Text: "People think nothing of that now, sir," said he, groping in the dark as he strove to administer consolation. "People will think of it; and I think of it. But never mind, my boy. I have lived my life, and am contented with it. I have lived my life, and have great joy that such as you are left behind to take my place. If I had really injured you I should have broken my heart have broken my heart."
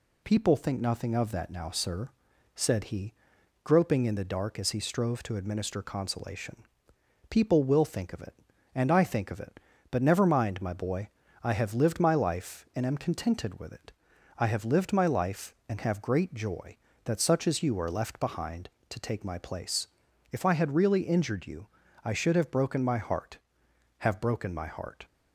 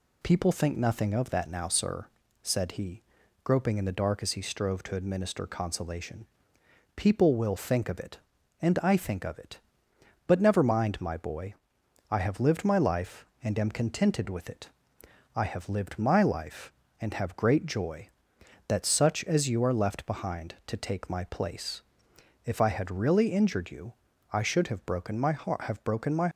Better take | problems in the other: first | pauses between "you" and "I"; at 23.9 s; 0.38 s long; also in the first // stops before "heart"; at 26.3 s

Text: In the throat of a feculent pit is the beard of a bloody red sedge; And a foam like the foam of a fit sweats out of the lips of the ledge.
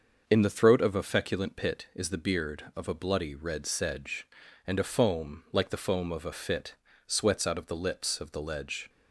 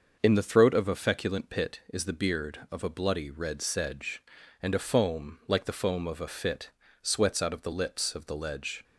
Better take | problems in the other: neither | starts louder than the rest; the same in both // pauses between "fit" and "sweats"; slight; the same in both

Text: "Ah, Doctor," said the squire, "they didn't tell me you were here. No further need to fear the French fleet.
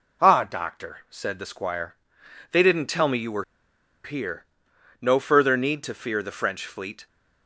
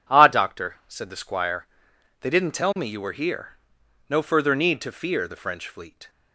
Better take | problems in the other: second | pauses between "were" and "here"; noticeable; at 3.4 s; 0.60 s long

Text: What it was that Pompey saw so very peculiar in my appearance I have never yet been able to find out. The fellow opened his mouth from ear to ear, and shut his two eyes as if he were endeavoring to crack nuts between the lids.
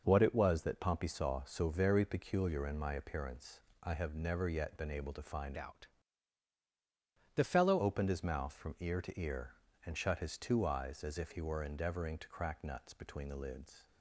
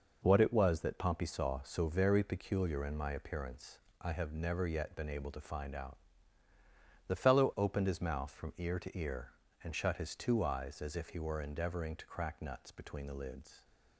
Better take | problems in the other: second | pauses between "appearance" and "I"; slight; at 3.6 s; 0.22 s long; slight in the second // changes voice from "out" to "fellow"; from 5.5 to 7.7 s; 2.2 s long

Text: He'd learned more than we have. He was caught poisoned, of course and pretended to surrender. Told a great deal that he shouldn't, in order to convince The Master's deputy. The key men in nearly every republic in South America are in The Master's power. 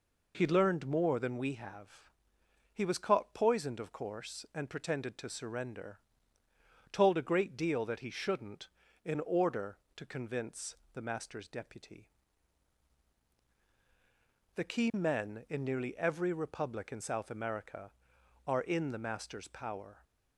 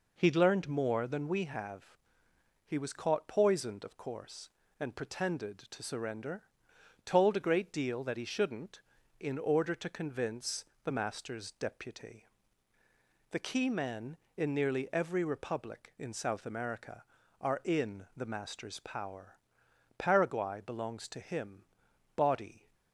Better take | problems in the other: first | pauses between "convince" and "The"; slight; at 10.6 s; 0.18 s long; slight in the first // goes on to say "Paraguay belongs to him body"; strong; from 19.9 s on; 2.7 s long

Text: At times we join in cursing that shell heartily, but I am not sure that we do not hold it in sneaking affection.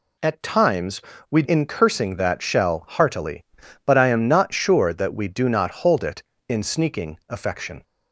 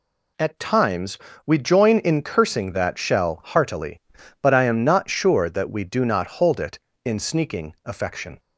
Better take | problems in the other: second | pauses between "times" and "we"; slight; at 0.9 s; 0.30 s long; slight in the second // skips "join"; at 1.4 s

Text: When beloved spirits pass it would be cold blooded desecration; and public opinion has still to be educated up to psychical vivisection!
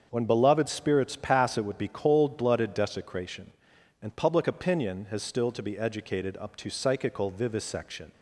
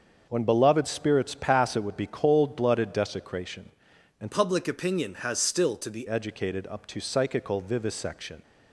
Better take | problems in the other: first | starts louder than the rest; until 1.2 s; 6.5 dB; also in the first // changes voice from "public" to "be"; from 4.3 to 6.0 s; 1.7 s long

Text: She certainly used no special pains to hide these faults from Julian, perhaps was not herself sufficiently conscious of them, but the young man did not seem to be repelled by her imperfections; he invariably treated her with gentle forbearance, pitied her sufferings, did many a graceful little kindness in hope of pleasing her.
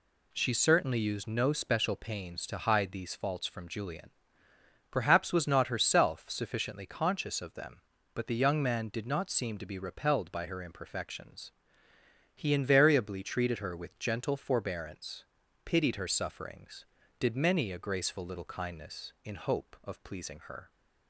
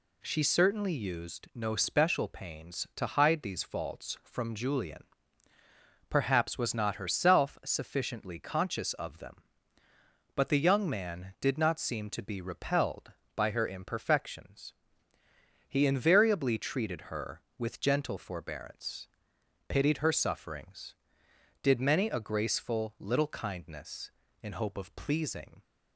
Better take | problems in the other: first | stops before "her"; at 25.6 s

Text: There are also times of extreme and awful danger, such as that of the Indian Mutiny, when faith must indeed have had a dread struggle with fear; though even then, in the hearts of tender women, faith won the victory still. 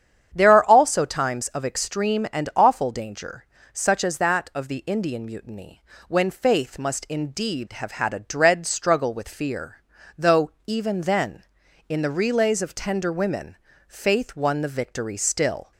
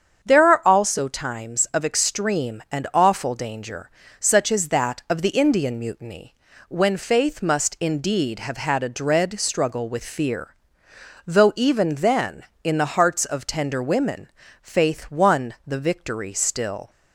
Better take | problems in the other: second | starts louder than the rest; strong; until 1.3 s; 8.5 dB; strong in the second // pauses between "though" and "even"; slight; at 10.5 s; 0.16 s long // says "relays" for "hearts"; at 12.1 s

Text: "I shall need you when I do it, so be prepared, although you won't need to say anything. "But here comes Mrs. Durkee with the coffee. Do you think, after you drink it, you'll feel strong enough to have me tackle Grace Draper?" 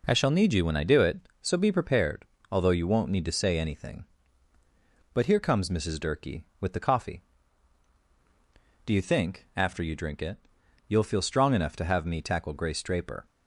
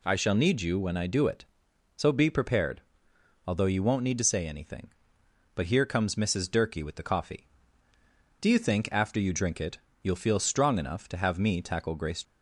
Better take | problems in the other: first | stops before "Draper"; at 12.2 s

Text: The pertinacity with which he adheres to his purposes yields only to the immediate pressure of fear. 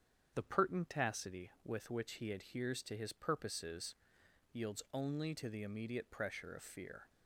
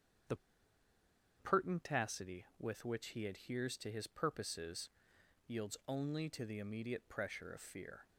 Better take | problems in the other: first | starts louder than the rest; strong; until 2.3 s; 8 dB; strong in the first // pauses between "The" and "pertinacity"; at 0.3 s; 1.0 s long // pauses between "purposes" and "yields"; noticeable; at 4.8 s; 0.58 s long; noticeable in the first

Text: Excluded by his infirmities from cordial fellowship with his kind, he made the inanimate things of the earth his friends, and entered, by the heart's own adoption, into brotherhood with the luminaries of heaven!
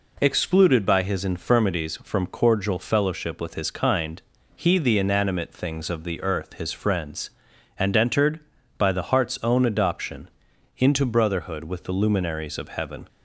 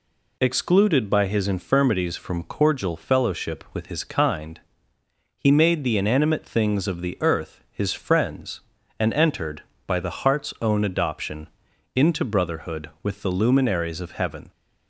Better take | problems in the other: second | skips "made"; at 4.7 s

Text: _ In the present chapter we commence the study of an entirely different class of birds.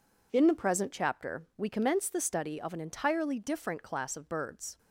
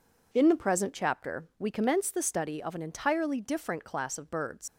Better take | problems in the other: first | leaves "birds" unfinished; at 4.6 s; 115 ms

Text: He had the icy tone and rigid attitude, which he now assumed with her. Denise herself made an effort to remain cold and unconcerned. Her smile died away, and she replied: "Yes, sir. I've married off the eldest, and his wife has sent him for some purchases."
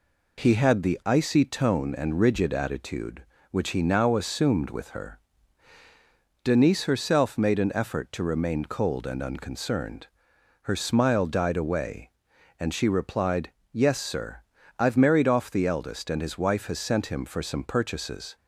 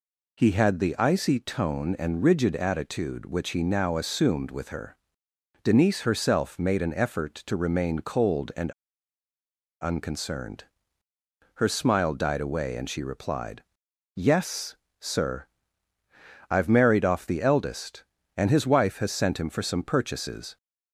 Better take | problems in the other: first | pauses between "and" and "unconcerned"; at 8.7 s; 1.1 s long

